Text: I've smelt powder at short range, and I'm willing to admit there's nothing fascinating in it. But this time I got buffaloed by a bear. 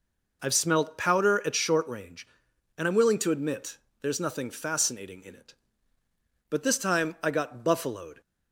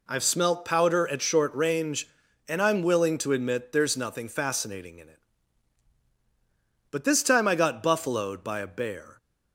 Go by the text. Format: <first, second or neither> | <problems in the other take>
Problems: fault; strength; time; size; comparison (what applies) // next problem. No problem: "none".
second | pauses between "admit" and "there's"; slight; at 3.7 s; 0.24 s long // stops before "by a bear"; at 8.2 s